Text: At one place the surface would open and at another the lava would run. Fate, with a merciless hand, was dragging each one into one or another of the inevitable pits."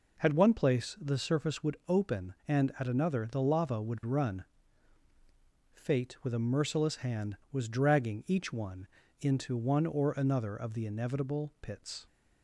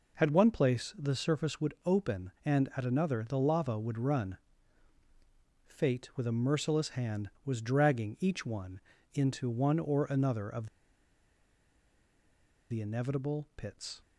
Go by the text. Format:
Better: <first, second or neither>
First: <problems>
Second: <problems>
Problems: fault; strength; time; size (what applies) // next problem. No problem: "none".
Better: first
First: pauses between "one" and "into"; slight; at 8.8 s; 0.34 s long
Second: pauses between "one" and "into"; slight; at 8.7 s; 0.34 s long // pauses between "of" and "the"; strong; at 10.6 s; 2.0 s long